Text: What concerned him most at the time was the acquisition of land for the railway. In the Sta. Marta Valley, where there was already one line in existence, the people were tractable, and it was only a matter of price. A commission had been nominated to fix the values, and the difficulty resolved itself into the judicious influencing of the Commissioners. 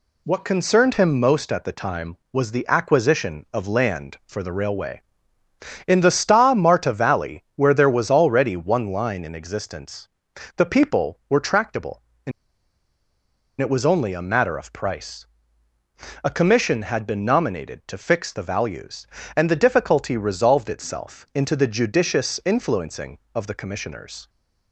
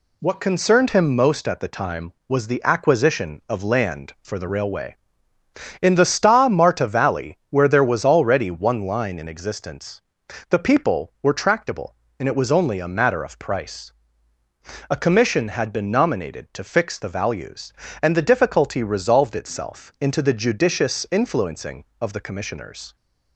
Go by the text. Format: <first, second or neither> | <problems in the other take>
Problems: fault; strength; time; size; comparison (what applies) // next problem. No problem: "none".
second | pauses between "and" and "it"; strong; at 12.3 s; 1.2 s long